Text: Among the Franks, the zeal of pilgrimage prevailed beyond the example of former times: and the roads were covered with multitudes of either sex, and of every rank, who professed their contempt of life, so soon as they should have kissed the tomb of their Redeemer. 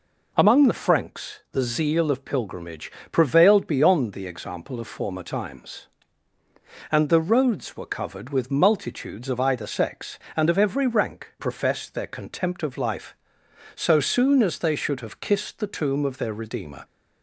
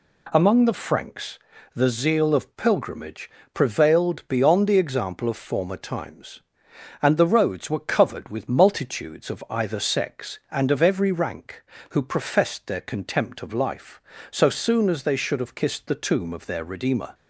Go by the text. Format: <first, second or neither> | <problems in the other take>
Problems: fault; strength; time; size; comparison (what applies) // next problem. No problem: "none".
second | pauses between "pilgrimage" and "prevailed"; slight; at 2.8 s; 0.22 s long; slight in the second // skips "who"; at 11.3 s